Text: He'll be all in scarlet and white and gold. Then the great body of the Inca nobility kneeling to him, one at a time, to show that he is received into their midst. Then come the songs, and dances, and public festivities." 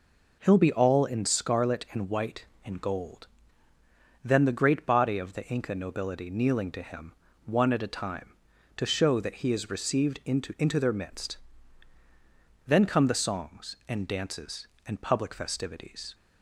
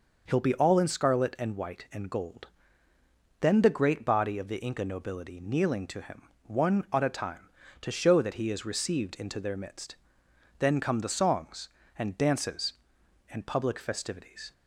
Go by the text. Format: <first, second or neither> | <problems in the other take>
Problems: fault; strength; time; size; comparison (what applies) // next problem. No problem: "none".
second | says "into" twice; at 10.5 s